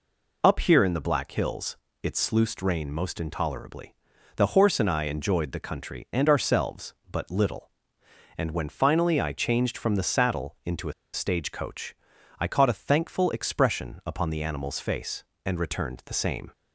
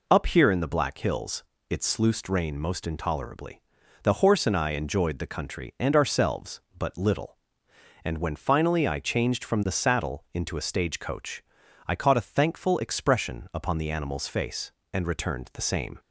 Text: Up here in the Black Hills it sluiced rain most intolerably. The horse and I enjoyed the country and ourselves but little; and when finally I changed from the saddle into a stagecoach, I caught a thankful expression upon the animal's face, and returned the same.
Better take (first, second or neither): second